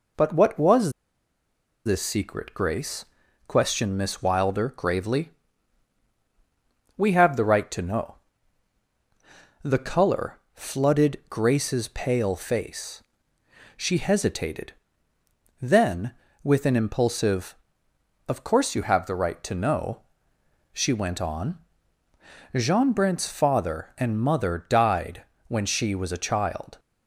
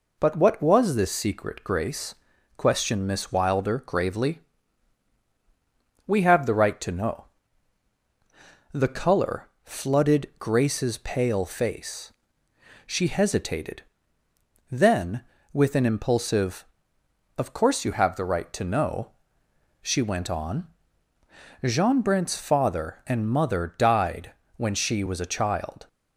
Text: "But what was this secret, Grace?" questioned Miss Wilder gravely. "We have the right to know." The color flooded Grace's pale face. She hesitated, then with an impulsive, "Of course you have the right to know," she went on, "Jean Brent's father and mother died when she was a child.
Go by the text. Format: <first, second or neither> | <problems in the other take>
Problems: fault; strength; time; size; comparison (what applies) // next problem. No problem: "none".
second | pauses between "was" and "this"; noticeable; at 0.9 s; 0.94 s long // pauses between "died" and "when"; slight; at 25.2 s; 0.24 s long; slight in the second